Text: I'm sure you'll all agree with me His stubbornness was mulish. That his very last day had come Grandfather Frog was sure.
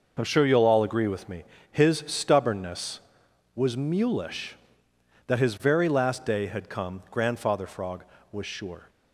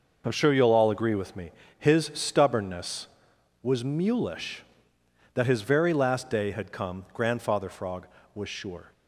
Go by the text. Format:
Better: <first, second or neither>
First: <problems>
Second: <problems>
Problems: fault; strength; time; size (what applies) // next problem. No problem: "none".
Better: neither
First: pauses between "me" and "His"; slight; at 1.4 s; 0.26 s long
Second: pauses between "me" and "His"; slight; at 1.5 s; 0.26 s long